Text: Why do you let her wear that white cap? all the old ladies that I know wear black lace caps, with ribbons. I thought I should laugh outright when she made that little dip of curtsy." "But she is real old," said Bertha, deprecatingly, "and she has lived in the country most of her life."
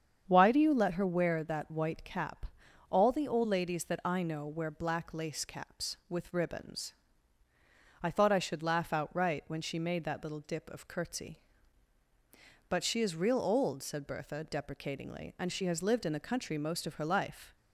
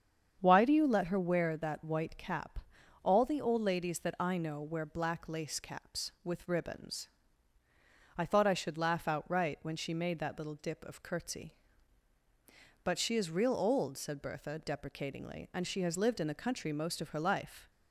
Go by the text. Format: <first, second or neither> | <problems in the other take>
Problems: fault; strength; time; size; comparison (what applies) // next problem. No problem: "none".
neither | starts louder than the rest; strong; the same in both